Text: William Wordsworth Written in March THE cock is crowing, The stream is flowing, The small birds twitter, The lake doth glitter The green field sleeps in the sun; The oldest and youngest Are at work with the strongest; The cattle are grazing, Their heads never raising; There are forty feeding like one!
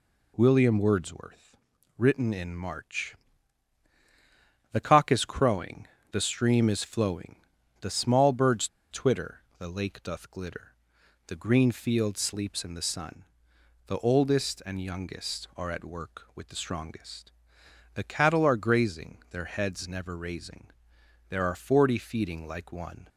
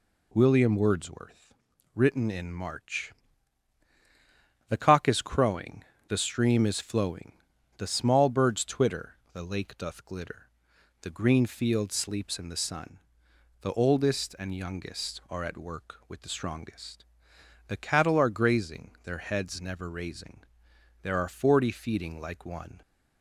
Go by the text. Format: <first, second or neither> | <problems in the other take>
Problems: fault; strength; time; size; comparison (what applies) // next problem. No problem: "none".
second | pauses between "Wordsworth" and "Written"; at 1.5 s; 0.40 s long; also in the second // pauses between "March" and "THE"; strong; at 3.1 s; 1.5 s long; strong in the second // pauses between "birds" and "twitter"; slight; at 8.6 s; 0.25 s long // pauses between "glitter" and "The"; noticeable; at 10.7 s; 0.54 s long; noticeable in the second